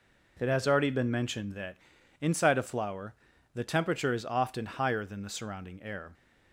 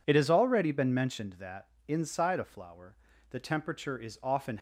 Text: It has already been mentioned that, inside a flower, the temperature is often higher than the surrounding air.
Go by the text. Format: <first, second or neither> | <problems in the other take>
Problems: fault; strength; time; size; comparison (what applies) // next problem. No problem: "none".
first | stops before "higher than the surrounding air"; at 4.5 s